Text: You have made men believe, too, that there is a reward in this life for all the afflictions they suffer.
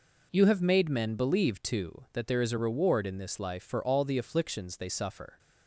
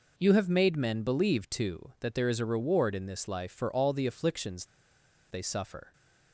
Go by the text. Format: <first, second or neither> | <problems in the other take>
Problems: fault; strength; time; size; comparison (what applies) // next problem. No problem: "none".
first | pauses between "afflictions" and "they"; noticeable; at 4.6 s; 0.66 s long